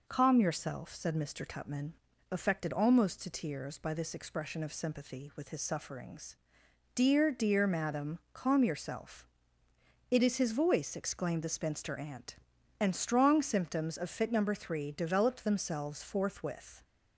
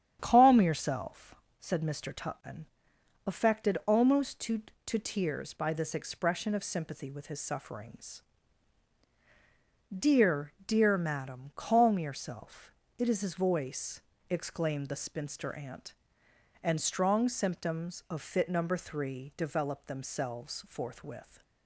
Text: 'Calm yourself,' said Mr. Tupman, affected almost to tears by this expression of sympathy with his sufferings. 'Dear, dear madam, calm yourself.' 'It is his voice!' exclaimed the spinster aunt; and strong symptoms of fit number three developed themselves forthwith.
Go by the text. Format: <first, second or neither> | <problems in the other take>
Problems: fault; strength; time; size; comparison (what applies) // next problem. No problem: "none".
first | starts louder than the rest; strong; until 1.2 s; 9 dB // says "to" twice; at 4.8 s